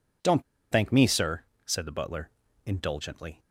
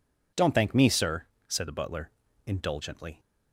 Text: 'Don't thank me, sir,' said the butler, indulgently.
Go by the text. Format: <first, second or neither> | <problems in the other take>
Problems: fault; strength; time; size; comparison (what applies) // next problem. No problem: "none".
second | pauses between "Don't" and "thank"; slight; at 0.4 s; 0.29 s long